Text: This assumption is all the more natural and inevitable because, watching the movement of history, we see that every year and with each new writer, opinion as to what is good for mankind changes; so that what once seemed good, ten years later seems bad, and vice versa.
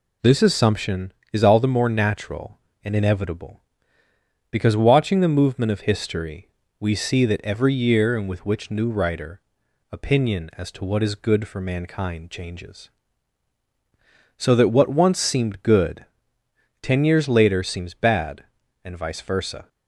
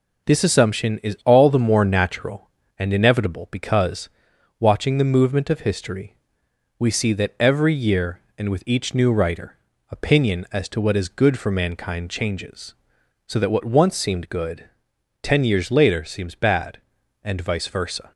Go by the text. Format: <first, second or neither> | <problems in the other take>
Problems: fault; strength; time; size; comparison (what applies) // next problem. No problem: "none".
second | says "which" for "each"; at 8.4 s